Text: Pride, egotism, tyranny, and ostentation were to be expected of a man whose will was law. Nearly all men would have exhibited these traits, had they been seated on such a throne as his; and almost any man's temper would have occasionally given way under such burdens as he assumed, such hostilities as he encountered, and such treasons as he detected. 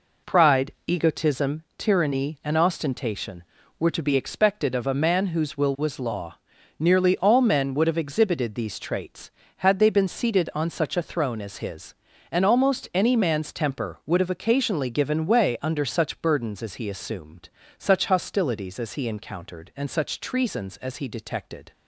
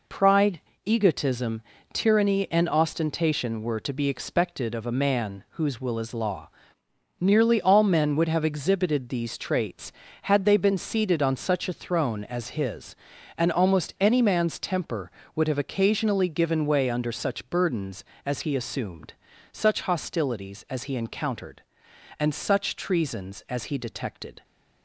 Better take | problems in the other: first | says "is" for "was"; at 5.9 s

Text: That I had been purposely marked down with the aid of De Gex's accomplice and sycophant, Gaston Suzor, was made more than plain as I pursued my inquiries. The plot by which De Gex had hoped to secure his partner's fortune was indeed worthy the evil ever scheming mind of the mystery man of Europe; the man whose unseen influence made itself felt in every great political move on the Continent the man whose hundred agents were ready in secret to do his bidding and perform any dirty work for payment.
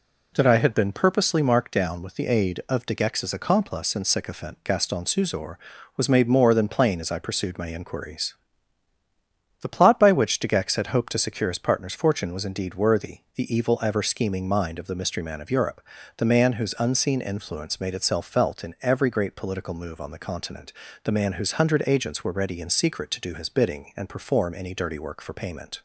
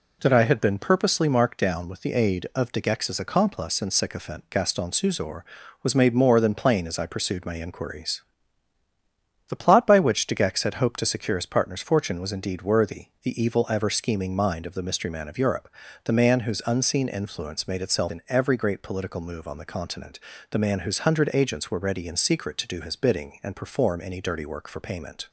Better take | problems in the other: first | pauses between "worthy" and "the"; slight; at 13.0 s; 0.16 s long; slight in the first // skips "felt"; at 18.1 s // pauses between "Continent" and "the"; slight; at 20.1 s; 0.32 s long; slight in the first

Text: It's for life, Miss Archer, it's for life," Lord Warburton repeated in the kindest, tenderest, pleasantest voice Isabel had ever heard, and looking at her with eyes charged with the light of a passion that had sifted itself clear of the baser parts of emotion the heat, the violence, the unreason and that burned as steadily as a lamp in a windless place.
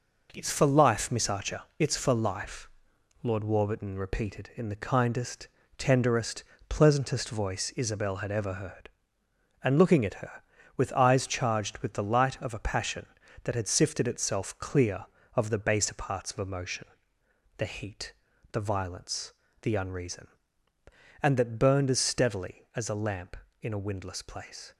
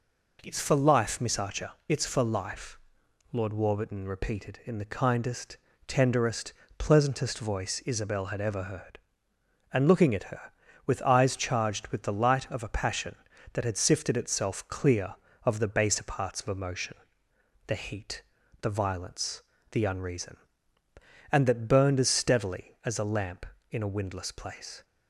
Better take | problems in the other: second | gets quieter; noticeable; throughout; 6 dB // pauses between "emotion" and "the"; noticeable; at 16.8 s; 0.70 s long; noticeable in the second

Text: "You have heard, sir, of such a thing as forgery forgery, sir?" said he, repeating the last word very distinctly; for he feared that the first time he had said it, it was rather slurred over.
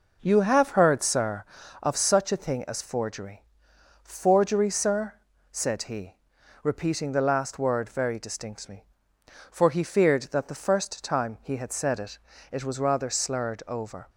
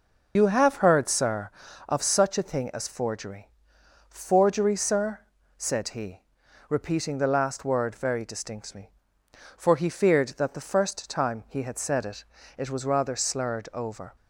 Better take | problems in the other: first | loses the start of "You"; at 0.3 s; 75 ms // pauses between "forgery" and "forgery"; noticeable; at 3.4 s; 0.60 s long; noticeable in the first

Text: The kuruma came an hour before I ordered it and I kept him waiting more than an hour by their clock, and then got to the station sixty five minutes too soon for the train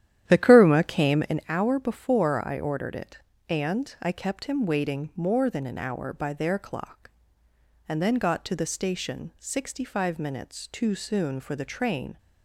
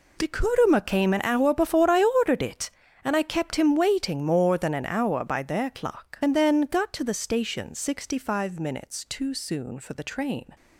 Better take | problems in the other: second | starts louder than the rest; strong; until 1.4 s; 11.5 dB

